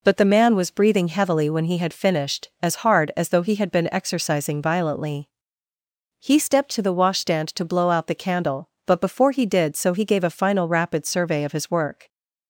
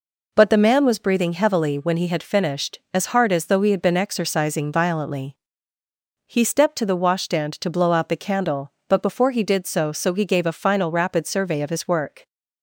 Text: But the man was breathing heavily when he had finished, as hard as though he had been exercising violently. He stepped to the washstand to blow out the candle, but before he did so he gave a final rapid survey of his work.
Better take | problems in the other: first | says "so" twice; at 9.9 s

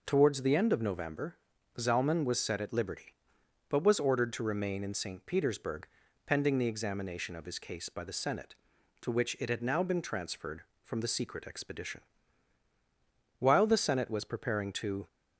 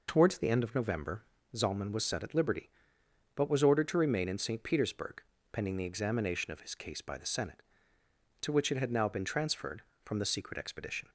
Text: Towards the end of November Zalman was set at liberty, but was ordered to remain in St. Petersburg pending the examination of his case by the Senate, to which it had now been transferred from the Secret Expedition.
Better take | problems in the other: second | pauses between "November" and "Zalman"; at 1.3 s; 0.42 s long; slight in the second // pauses between "Petersburg" and "pending"; at 5.8 s; 0.40 s long; slight in the second // goes on to say "While the Senate was preparing to"; strong; from 13.3 s on; 1.6 s long

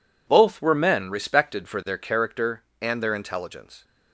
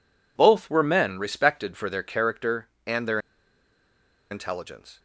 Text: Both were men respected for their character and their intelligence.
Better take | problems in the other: first | pauses between "their" and "intelligence"; at 3.1 s; 1.1 s long

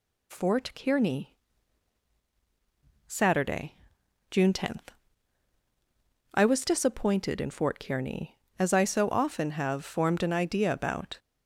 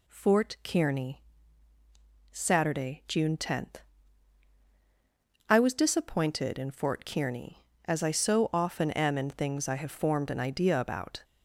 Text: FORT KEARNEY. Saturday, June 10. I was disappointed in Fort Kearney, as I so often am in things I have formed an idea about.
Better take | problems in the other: second | skips "am in things I"; at 9.5 s

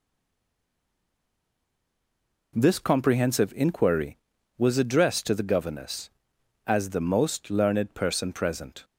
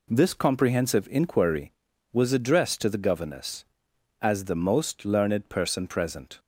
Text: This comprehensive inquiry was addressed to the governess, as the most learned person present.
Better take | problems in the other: second | stays silent before the first word; until 2.5 s; 2.5 s long

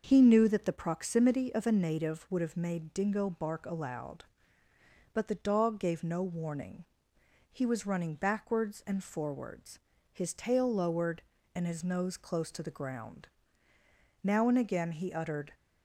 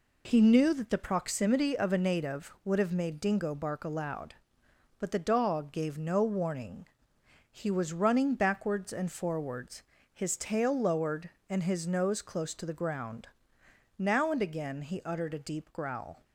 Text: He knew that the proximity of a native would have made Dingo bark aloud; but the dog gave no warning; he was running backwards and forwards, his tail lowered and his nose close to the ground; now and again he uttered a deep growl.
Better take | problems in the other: second | starts louder than the rest; until 1.0 s; 6.5 dB // stops before "a deep growl"; at 15.5 s

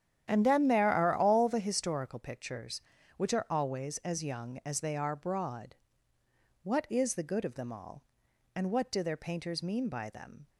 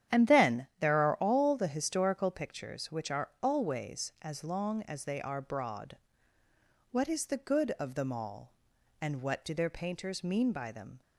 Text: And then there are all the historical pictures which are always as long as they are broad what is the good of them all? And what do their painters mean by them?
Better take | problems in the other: second | starts louder than the rest; strong; until 1.2 s; 10 dB; strong in the second // says "young" for "long"; at 4.2 s // pauses between "broad" and "what"; noticeable; at 5.7 s; 0.88 s long; noticeable in the second

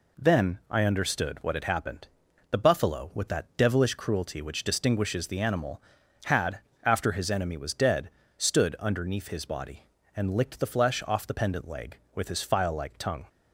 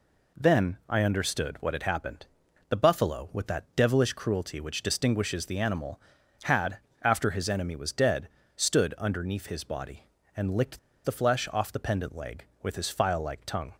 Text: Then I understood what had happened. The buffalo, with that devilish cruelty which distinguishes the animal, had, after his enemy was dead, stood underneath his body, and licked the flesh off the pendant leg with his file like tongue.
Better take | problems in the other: first | pauses between "licked" and "the"; slight; at 10.7 s; 0.25 s long

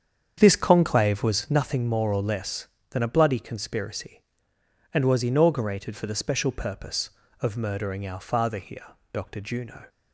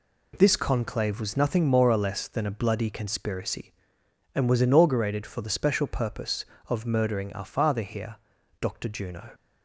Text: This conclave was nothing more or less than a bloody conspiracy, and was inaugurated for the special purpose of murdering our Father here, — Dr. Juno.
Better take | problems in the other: second | starts louder than the rest; strong; until 1.6 s; 8 dB

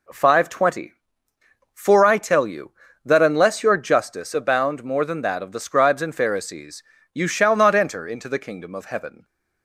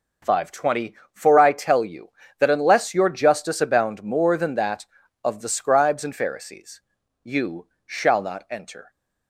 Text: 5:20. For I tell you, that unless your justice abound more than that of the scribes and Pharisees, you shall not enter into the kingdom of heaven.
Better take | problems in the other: first | pauses between "you" and "shall"; slight; at 7.6 s; 0.18 s long // stops before "into the kingdom of heaven"; at 8.9 s

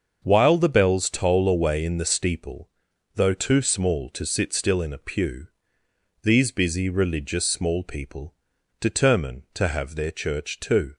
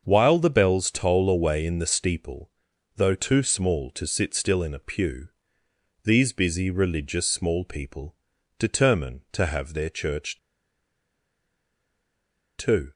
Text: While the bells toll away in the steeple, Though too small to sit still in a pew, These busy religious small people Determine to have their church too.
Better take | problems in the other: first | starts louder than the rest; until 1.0 s; 6.5 dB; also in the first // pauses between "people" and "Determine"; at 8.1 s; 0.44 s long; noticeable in the first // pauses between "church" and "too"; strong; at 10.3 s; 2.2 s long

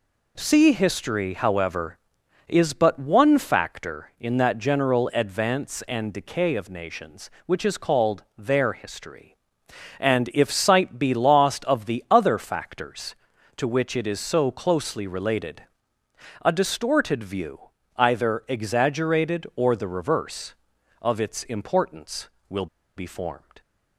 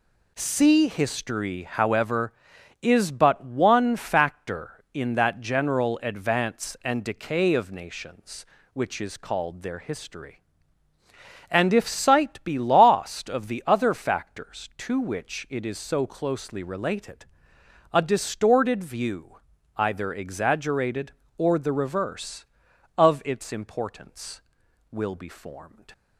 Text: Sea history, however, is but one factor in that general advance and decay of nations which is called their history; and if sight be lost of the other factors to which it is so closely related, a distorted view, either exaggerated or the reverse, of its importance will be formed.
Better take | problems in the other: second | pauses between "will" and "be"; slight; at 22.6 s; 0.30 s long

